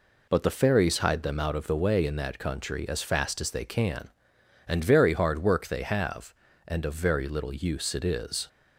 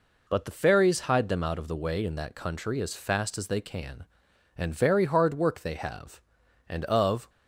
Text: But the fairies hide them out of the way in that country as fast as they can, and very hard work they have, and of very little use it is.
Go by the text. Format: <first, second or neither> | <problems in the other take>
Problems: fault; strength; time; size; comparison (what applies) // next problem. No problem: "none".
first | stops before "very little use it is"; at 7.2 s